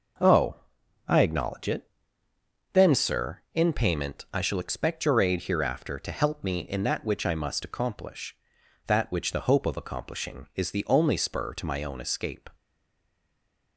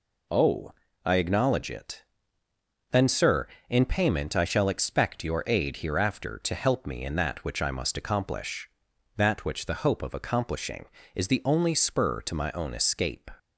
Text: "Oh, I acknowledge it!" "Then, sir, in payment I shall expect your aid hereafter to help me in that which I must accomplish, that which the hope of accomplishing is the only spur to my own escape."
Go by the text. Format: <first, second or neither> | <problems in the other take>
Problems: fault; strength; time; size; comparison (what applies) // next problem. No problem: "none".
second | stays silent after the last word; noticeable; from 12.5 s on; 1.2 s long